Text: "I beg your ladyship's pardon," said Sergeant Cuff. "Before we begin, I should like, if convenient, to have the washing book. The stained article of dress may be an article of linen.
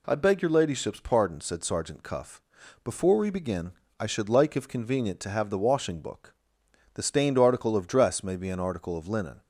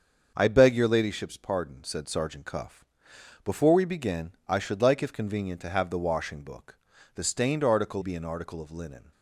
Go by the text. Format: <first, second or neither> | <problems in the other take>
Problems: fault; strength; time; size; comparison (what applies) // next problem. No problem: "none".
first | starts louder than the rest; until 1.3 s; 6.5 dB // skips "of dress may"; at 8.0 s